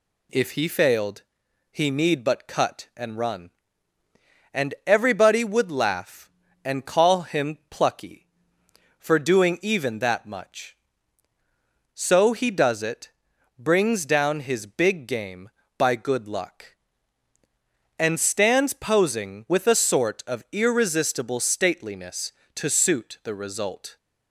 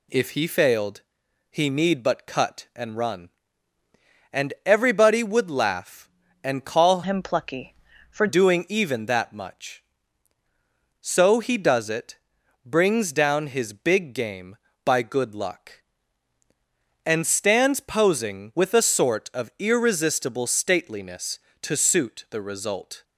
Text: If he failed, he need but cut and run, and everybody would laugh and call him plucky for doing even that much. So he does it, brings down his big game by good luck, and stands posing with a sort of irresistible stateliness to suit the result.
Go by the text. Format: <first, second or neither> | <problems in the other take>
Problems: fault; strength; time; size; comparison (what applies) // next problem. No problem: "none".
first | changes voice from "him" to "for"; from 7.0 to 8.2 s; 1.2 s long